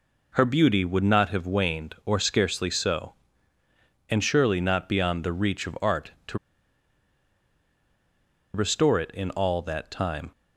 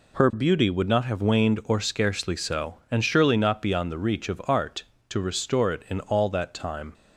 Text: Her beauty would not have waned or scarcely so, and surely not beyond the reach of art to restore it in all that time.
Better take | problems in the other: second | pauses between "to" and "restore"; strong; at 6.3 s; 2.1 s long

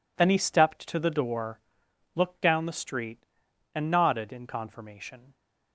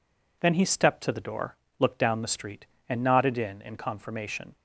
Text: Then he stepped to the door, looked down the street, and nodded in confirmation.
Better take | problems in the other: first | says "in" twice; at 3.6 s

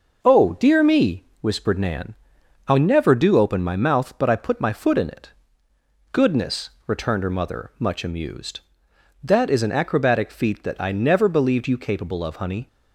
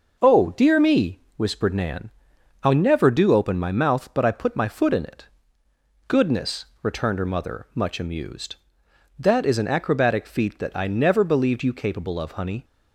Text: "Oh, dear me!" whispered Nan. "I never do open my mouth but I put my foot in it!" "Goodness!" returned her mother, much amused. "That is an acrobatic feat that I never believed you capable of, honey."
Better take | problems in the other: neither | none

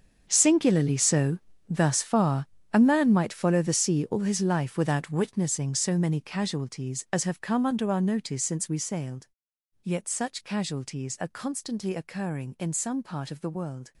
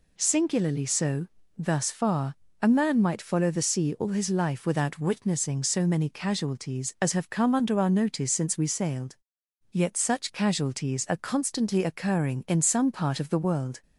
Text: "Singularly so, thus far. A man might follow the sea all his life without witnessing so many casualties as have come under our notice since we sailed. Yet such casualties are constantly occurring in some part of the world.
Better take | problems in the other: second | gets quieter; strong; throughout; 16 dB

